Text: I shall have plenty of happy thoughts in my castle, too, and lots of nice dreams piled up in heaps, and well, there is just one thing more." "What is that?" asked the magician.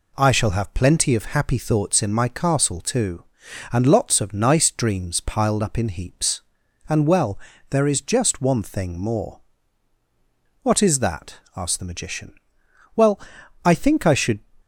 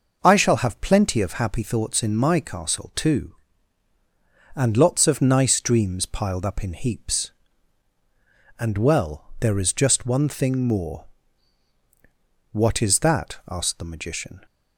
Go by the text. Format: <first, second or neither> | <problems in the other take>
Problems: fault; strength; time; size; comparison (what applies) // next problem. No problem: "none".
second | goes on to say "Well I think I should"; from 12.9 s on; 1.4 s long